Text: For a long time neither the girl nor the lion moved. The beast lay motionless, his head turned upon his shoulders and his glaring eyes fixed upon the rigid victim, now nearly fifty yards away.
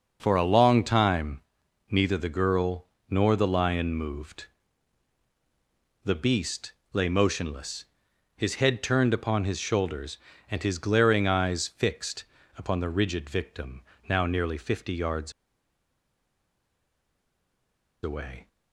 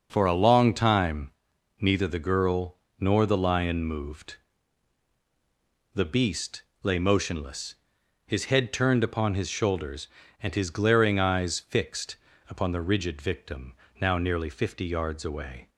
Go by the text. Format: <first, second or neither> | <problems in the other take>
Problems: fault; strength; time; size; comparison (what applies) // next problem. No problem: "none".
second | pauses between "time" and "neither"; noticeable; at 1.4 s; 0.48 s long; noticeable in the second // pauses between "girl" and "nor"; slight; at 2.8 s; 0.24 s long; slight in the second // pauses between "beast" and "lay"; slight; at 6.7 s; 0.20 s long; slight in the second // pauses between "fixed" and "upon"; slight; at 12.2 s; 0.30 s long; slight in the second // pauses between "yards" and "away"; strong; at 15.3 s; 2.7 s long